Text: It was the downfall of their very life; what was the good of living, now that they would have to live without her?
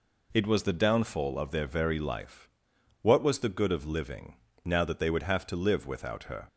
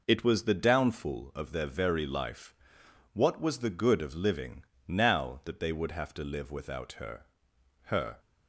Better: first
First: none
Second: says "her" twice; at 7.8 s

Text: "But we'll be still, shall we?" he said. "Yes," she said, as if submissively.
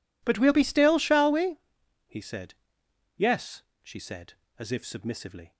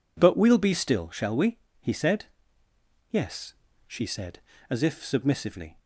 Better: neither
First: none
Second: none

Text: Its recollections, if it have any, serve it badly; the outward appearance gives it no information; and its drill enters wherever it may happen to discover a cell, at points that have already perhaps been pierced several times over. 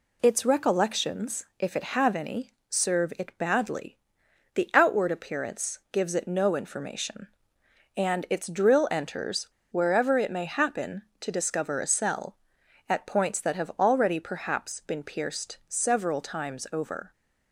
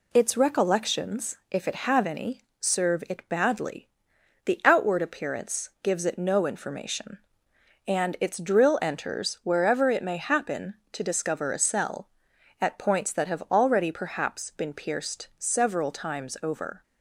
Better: second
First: pauses between "enters" and "wherever"; slight; at 9.4 s; 0.24 s long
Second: none

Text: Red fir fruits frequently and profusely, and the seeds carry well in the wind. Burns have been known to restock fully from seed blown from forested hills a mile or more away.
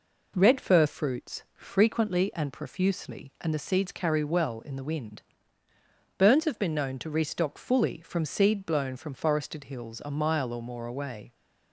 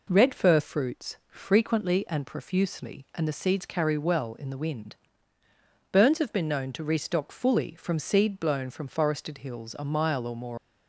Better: first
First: none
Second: stops before "away"; at 10.5 s

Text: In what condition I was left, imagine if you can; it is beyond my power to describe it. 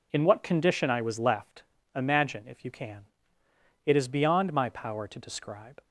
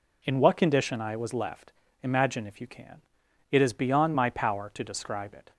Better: second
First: stops before "it"; at 5.8 s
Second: none

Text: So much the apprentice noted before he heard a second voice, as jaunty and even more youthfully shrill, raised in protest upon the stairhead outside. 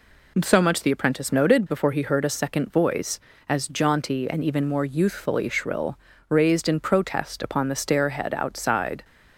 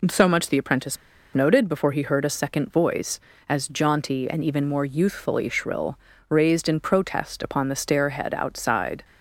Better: first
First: none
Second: pauses between "apprentice" and "noted"; at 0.9 s; 0.37 s long

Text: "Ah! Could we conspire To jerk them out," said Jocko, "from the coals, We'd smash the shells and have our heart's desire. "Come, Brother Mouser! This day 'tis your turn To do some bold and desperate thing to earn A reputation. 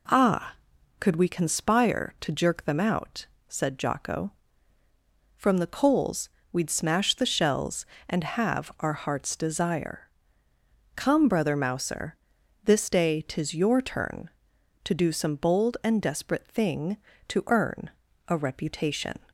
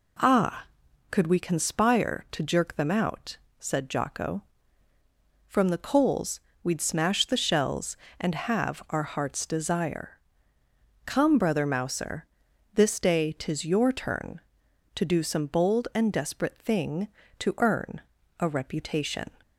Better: neither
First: pauses between "earn" and "A"; at 17.8 s; 0.39 s long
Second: pauses between "earn" and "A"; at 18.0 s; 0.40 s long

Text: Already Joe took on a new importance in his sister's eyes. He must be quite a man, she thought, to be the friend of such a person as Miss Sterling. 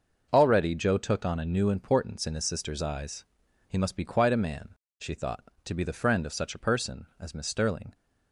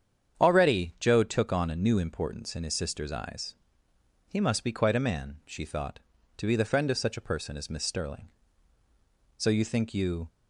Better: first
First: starts louder than the rest; noticeable; until 1.3 s; 6 dB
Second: starts louder than the rest; strong; until 1.4 s; 8 dB // goes on to say "So you think you"; noticeable; from 9.3 s on; 0.90 s long

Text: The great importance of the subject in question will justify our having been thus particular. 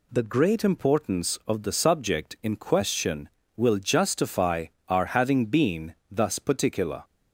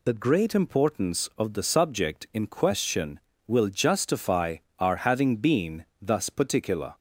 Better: first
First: pauses between "justify" and "our"; slight; at 4.6 s; 0.22 s long // pauses between "been" and "thus"; slight; at 5.9 s; 0.16 s long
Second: loses the start of "The"; at 0.0 s; 50 ms // pauses between "justify" and "our"; slight; at 4.5 s; 0.22 s long // pauses between "been" and "thus"; slight; at 5.8 s; 0.16 s long

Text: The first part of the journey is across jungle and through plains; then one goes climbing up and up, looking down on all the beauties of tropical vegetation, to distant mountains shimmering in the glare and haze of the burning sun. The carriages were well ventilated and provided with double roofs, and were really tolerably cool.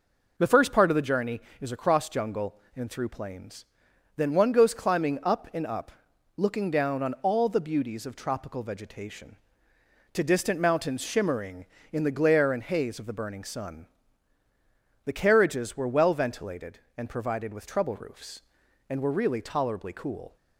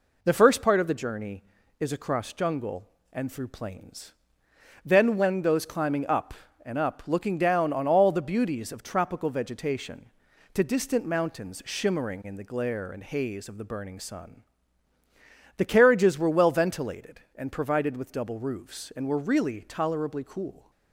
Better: second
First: says "trouble" for "double"; at 17.6 s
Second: none

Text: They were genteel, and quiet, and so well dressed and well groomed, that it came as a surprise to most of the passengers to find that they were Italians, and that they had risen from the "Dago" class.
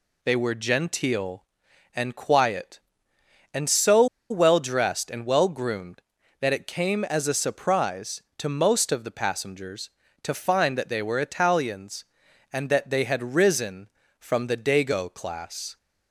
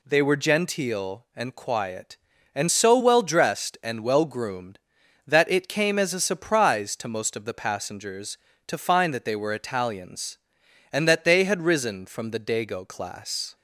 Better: second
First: pauses between "so" and "well"; slight; at 4.0 s; 0.24 s long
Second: none

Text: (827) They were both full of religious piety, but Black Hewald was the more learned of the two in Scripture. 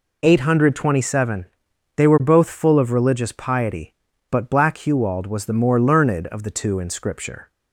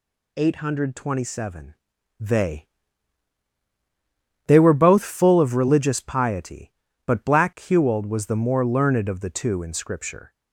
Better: first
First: none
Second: says "They" twice; at 4.4 s

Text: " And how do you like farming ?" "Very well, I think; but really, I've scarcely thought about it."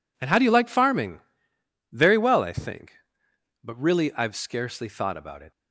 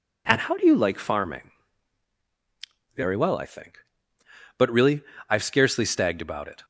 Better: first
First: none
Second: says "stagged" for "thought"; at 5.8 s

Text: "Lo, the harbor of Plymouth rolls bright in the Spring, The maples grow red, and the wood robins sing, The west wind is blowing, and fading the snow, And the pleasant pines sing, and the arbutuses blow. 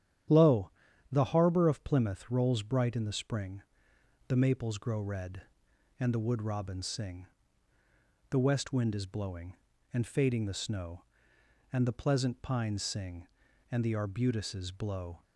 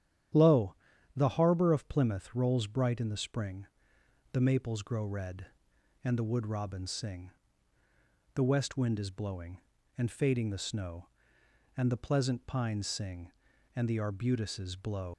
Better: first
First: starts louder than the rest; strong; until 1.7 s; 10.5 dB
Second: starts louder than the rest; strong; until 1.7 s; 10.5 dB // leaves "blow" unfinished; at 15.1 s; 135 ms

